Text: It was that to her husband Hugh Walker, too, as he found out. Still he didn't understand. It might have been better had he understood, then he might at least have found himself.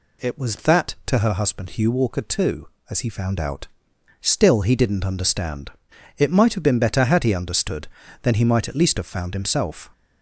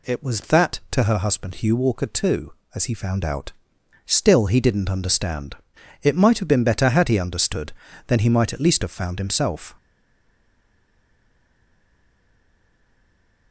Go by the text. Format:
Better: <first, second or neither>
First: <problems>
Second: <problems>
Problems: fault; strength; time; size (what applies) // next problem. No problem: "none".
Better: first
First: none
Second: stays silent after the last word; strong; from 9.7 s on; 3.8 s long